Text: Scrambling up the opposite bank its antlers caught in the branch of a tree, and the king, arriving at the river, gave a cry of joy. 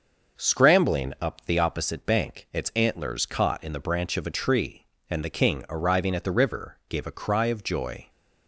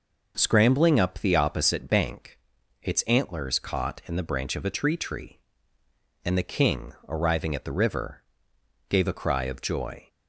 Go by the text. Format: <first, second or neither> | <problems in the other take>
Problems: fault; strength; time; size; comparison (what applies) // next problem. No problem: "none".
first | pauses between "bank" and "its"; at 2.3 s; 0.44 s long // says "tree" twice; at 4.9 s